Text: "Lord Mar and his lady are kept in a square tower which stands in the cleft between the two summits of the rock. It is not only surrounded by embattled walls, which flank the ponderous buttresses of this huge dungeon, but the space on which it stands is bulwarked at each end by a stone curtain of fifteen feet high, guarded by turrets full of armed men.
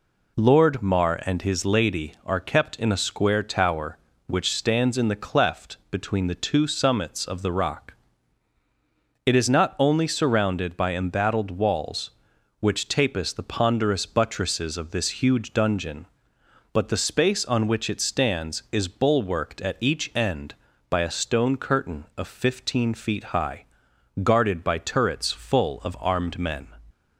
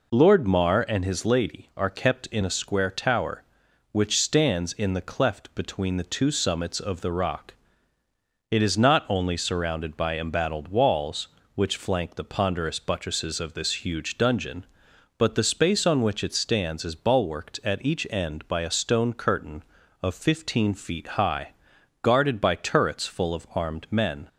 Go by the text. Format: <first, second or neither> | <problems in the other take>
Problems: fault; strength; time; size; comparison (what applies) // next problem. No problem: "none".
second | pauses between "cleft" and "between"; slight; at 5.7 s; 0.16 s long // says "tapis" for "flank"; at 12.8 s